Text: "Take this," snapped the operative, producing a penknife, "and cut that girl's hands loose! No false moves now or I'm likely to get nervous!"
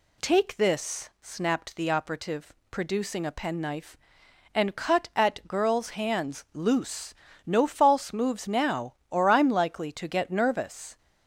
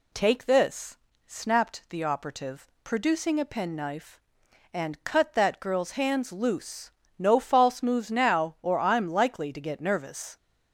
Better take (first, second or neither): second